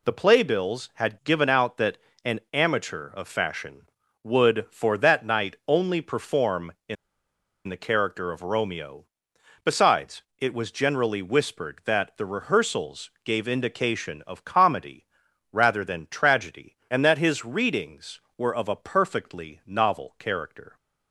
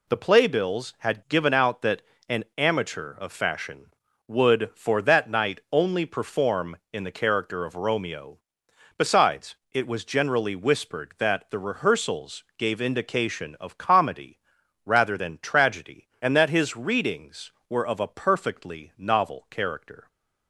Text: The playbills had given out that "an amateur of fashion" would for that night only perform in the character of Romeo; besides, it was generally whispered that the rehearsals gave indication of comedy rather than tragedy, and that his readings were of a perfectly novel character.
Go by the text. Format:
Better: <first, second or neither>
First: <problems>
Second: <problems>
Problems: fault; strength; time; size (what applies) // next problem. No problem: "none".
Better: second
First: pauses between "that" and "an"; slight; at 1.9 s; 0.30 s long // pauses between "in" and "the"; noticeable; at 6.9 s; 0.72 s long // pauses between "comedy" and "rather"; noticeable; at 15.0 s; 0.48 s long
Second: pauses between "that" and "an"; slight; at 2.0 s; 0.30 s long // pauses between "comedy" and "rather"; noticeable; at 14.3 s; 0.48 s long